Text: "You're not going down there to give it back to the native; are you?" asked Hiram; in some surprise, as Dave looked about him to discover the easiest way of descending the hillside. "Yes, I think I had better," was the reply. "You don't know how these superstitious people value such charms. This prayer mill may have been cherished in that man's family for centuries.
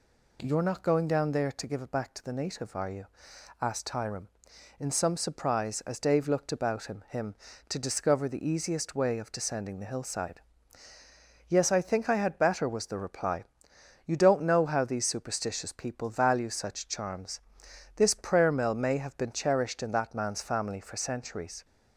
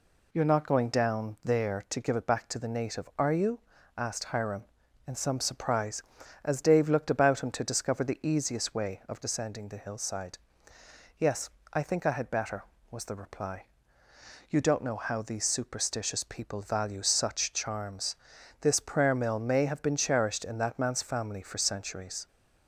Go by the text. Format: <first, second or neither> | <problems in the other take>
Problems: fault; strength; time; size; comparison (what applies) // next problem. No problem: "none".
second | says "him" twice; at 7.0 s